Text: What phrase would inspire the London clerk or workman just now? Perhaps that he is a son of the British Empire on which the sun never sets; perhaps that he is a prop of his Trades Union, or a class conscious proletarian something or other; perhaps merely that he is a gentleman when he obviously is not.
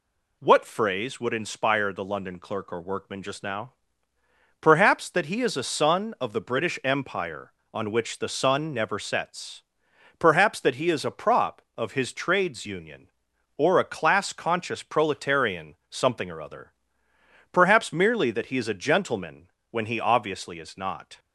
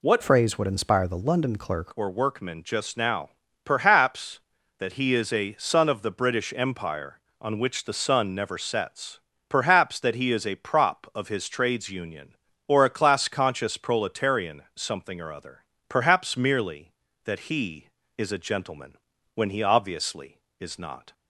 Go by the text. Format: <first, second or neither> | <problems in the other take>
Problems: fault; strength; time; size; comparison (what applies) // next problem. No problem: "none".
first | changes voice from "phrase" to "clerk"; from 0.2 to 1.9 s; 1.7 s long // pauses between "gentleman" and "when"; at 18.9 s; 0.38 s long; slight in the first